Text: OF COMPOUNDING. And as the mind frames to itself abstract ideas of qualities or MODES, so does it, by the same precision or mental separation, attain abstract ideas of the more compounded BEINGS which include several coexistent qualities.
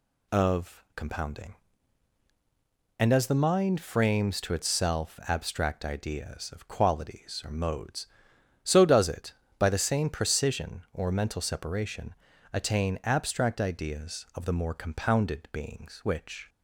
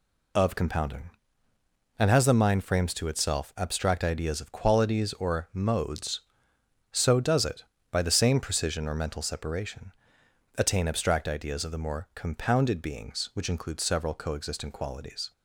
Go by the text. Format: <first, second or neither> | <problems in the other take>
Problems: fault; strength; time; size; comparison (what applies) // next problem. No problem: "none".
second | stops before "include several coexistent qualities"; at 16.4 s